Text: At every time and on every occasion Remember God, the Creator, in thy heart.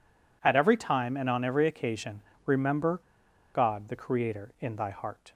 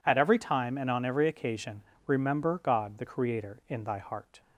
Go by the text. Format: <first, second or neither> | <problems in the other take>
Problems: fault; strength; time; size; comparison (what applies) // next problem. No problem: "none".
second | pauses between "occasion" and "Remember"; slight; at 2.2 s; 0.22 s long; slight in the second // pauses between "Remember" and "God"; noticeable; at 2.9 s; 0.57 s long